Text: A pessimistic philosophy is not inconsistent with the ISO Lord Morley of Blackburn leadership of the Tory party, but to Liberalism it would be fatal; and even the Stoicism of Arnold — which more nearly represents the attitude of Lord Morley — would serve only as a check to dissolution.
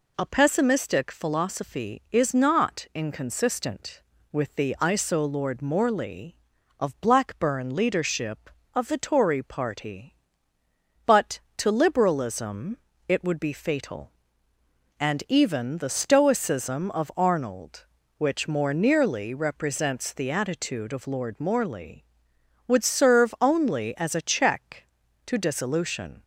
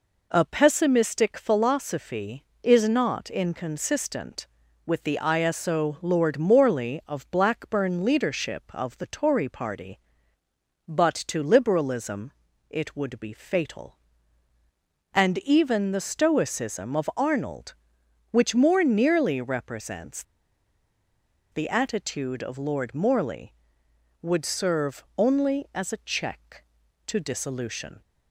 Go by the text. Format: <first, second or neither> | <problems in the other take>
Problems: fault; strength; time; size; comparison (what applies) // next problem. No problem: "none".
first | pauses between "Liberalism" and "it"; slight; at 12.3 s; 0.36 s long; slight in the first // pauses between "represents" and "the"; strong; at 20.2 s; 1.2 s long // pauses between "serve" and "only"; slight; at 25.0 s; 0.16 s long